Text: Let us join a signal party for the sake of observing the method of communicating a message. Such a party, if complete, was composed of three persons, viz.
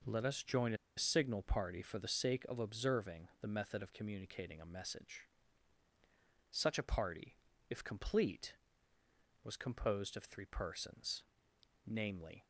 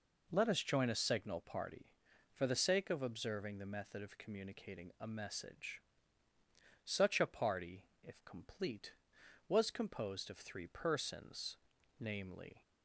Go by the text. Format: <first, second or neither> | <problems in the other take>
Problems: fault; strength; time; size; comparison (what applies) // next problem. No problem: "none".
second | pauses between "a" and "signal"; slight; at 0.7 s; 0.21 s long